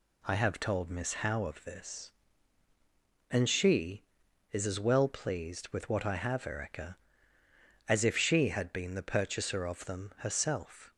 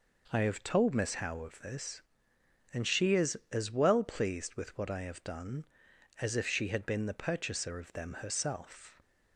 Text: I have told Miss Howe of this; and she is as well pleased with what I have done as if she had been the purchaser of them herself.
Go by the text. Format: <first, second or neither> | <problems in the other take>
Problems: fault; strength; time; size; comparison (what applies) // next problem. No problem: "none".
second | says "erica" for "done"; at 6.4 s